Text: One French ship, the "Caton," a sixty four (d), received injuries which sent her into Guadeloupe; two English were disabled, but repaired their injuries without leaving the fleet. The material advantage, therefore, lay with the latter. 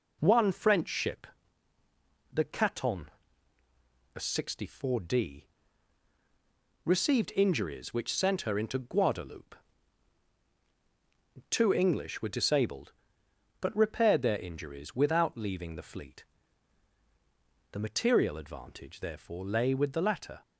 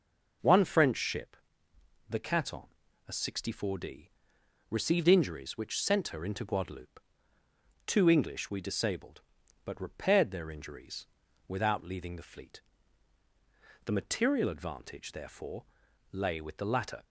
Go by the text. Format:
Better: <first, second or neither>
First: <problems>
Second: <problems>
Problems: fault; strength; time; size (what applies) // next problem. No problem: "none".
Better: first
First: none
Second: says "we" for "were"; at 8.4 s // pauses between "injuries" and "without"; at 11.0 s; 0.38 s long